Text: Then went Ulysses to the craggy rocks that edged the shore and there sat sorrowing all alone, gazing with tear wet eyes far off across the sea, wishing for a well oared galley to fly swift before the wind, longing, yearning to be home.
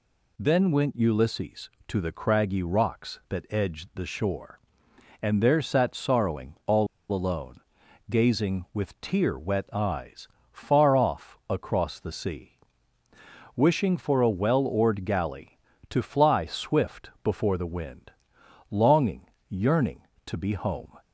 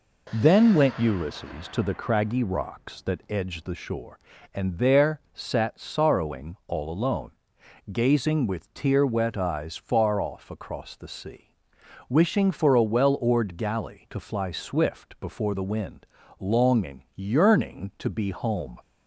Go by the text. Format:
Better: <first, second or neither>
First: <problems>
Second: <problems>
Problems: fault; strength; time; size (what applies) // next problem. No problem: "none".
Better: second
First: pauses between "all" and "alone"; slight; at 6.8 s; 0.25 s long // pauses between "eyes" and "far"; slight; at 10.2 s; 0.24 s long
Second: none